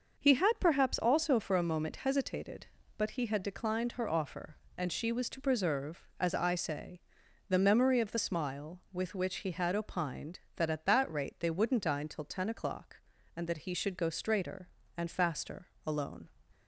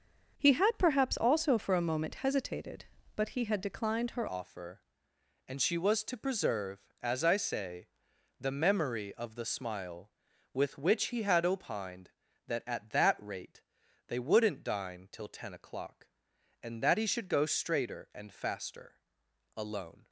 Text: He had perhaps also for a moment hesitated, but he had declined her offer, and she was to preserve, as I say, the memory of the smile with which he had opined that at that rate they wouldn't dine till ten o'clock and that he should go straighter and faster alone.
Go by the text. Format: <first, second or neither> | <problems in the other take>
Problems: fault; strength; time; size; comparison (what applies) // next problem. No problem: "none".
first | starts louder than the rest; until 1.4 s; 6.5 dB; noticeable in the first // changes voice at "offer"; from 4.2 s on; 15.8 s long // pauses between "rate" and "they"; at 13.6 s; 0.44 s long // pauses between "faster" and "alone"; noticeable; at 18.9 s; 0.56 s long; slight in the first